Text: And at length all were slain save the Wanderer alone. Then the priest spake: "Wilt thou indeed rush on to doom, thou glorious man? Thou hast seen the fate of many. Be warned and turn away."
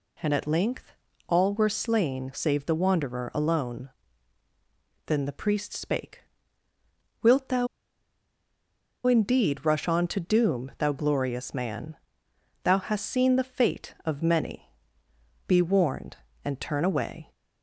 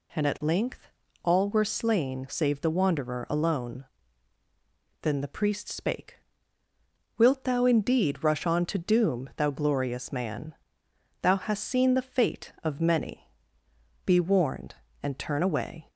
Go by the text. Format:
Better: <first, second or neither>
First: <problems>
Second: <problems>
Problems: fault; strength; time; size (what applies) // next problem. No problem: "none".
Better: second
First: pauses between "length" and "all"; slight; at 0.9 s; 0.36 s long // pauses between "thou" and "indeed"; strong; at 7.6 s; 1.3 s long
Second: pauses between "length" and "all"; slight; at 0.8 s; 0.36 s long